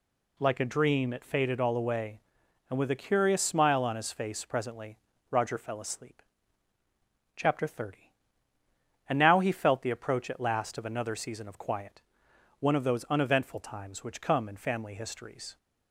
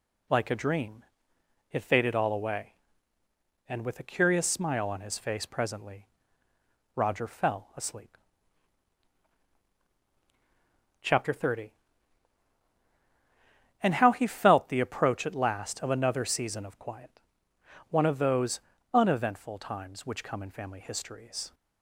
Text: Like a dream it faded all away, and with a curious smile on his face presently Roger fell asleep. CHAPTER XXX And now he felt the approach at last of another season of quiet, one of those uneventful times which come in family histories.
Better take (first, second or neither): first